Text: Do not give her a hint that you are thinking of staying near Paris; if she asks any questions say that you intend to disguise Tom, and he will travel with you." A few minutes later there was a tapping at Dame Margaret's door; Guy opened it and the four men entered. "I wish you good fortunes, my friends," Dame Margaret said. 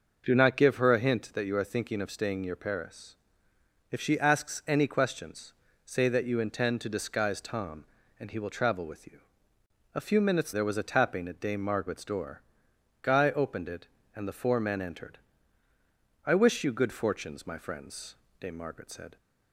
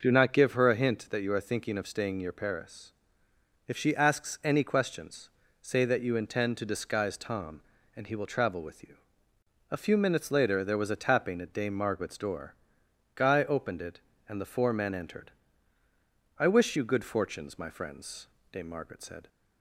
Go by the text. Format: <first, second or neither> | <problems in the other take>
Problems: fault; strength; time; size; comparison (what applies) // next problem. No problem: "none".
second | pauses between "questions" and "say"; slight; at 5.5 s; 0.32 s long; slight in the second // skips "later"; at 10.5 s